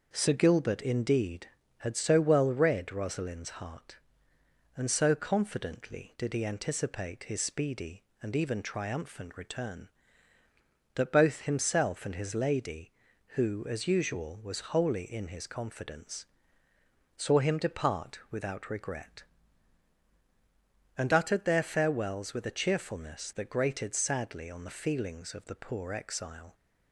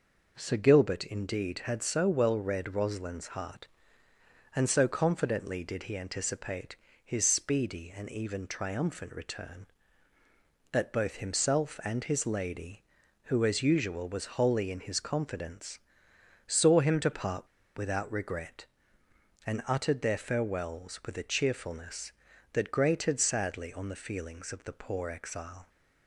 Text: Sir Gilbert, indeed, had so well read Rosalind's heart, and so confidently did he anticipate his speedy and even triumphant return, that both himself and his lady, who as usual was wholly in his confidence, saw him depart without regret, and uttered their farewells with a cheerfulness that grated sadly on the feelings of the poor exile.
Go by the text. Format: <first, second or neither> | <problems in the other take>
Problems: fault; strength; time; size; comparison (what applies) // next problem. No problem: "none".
first | pauses between "anticipate" and "his"; slight; at 6.7 s; 0.26 s long // pauses between "depart" and "without"; slight; at 17.4 s; 0.29 s long